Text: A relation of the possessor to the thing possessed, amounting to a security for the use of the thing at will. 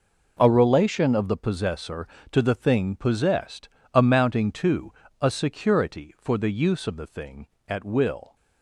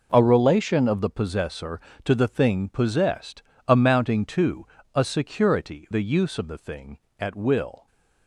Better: first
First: pauses between "to" and "a"; slight; at 4.9 s; 0.26 s long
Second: pauses between "to" and "a"; slight; at 4.6 s; 0.26 s long // skips "for"; at 5.8 s

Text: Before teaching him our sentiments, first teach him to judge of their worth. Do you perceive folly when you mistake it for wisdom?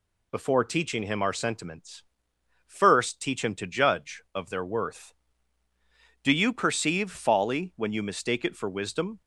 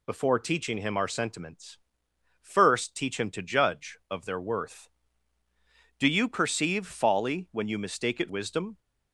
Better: first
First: none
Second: skips "for"; at 8.2 s

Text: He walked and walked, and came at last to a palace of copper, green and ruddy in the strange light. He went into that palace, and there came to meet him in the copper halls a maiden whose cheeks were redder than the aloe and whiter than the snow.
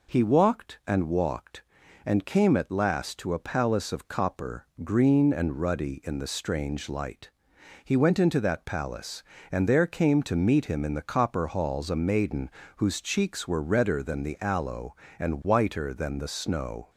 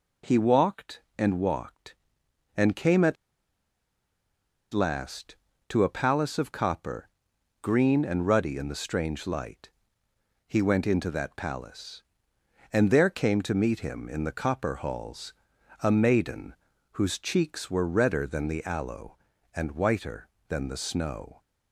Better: first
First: pauses between "maiden" and "whose"; slight; at 12.4 s; 0.28 s long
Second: pauses between "at" and "last"; strong; at 3.1 s; 1.5 s long // pauses between "halls" and "a"; noticeable; at 15.3 s; 0.50 s long // pauses between "maiden" and "whose"; at 16.5 s; 0.38 s long

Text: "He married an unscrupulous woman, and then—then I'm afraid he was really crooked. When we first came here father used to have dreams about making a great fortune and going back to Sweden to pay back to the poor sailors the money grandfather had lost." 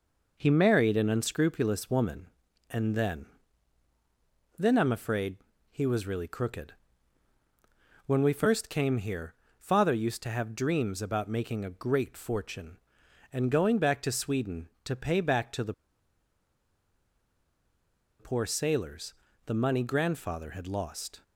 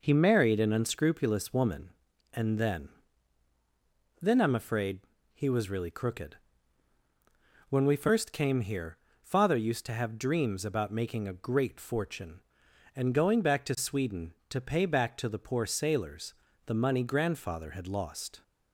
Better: second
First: pauses between "afraid" and "he"; slight; at 5.3 s; 0.34 s long // pauses between "here" and "father"; slight; at 9.3 s; 0.24 s long // pauses between "the" and "poor"; strong; at 15.7 s; 2.4 s long // pauses between "sailors" and "the"; slight; at 19.1 s; 0.32 s long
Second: pauses between "afraid" and "he"; slight; at 5.0 s; 0.34 s long // pauses between "here" and "father"; slight; at 8.9 s; 0.24 s long // pauses between "sailors" and "the"; slight; at 16.3 s; 0.32 s long

